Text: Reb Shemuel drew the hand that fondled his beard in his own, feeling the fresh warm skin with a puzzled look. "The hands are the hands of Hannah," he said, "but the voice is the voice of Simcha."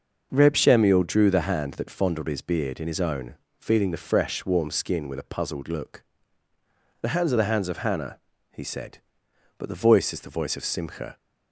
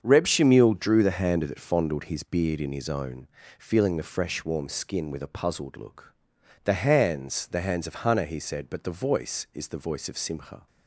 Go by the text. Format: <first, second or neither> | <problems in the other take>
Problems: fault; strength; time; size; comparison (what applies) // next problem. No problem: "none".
first | starts louder than the rest; strong; until 1.0 s; 7 dB; noticeable in the first // skips "are"; at 7.4 s